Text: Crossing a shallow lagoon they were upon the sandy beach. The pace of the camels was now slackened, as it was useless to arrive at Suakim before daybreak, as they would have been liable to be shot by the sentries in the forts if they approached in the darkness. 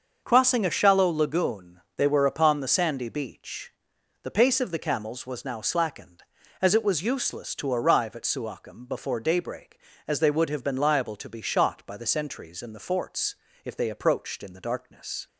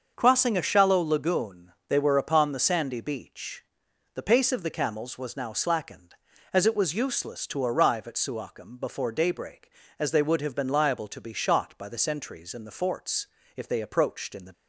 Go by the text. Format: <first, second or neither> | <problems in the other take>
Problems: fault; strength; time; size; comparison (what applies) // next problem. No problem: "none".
first | starts louder than the rest; until 1.1 s; 6.5 dB; also in the first // pauses between "lagoon" and "they"; slight; at 1.7 s; 0.16 s long; slight in the first // pauses between "forts" and "if"; slight; at 13.2 s; 0.30 s long; slight in the first // stops before "darkness"; at 14.5 s